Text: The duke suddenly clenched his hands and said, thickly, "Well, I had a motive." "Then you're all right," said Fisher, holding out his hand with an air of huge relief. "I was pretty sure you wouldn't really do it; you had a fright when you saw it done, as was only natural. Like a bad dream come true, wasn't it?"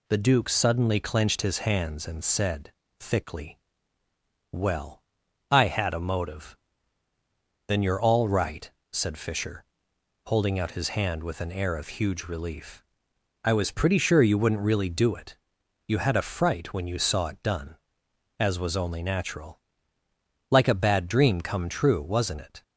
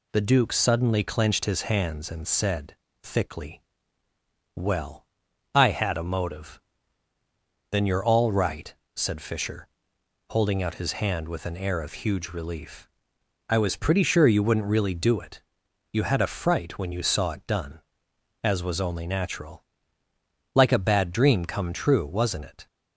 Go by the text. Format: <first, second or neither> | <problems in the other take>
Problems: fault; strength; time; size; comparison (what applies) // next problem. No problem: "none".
neither | none